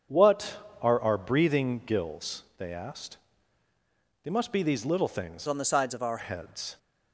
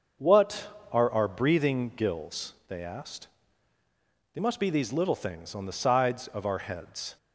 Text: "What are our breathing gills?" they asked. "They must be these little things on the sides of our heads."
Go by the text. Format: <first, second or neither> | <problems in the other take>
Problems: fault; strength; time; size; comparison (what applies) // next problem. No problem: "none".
second | starts louder than the rest; strong; until 1.3 s; 7.5 dB; also in the second // changes voice from "on" to "our"; from 5.4 to 6.1 s; 0.7 s long